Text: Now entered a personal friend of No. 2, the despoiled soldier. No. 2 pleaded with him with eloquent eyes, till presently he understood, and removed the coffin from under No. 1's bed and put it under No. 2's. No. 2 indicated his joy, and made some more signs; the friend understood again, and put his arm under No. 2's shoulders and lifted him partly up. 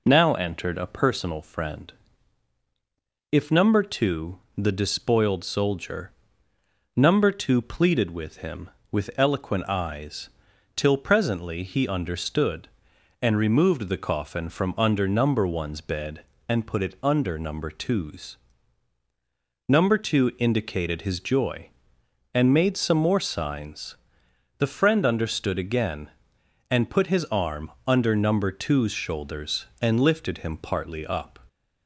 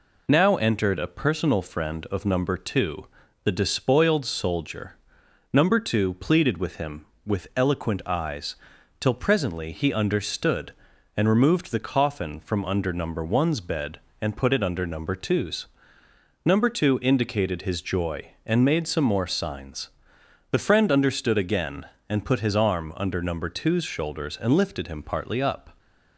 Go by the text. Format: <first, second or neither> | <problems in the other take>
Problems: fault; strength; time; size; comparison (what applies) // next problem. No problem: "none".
second | says "if" for "of"; at 3.3 s // pauses between "arm" and "under"; slight; at 27.7 s; 0.16 s long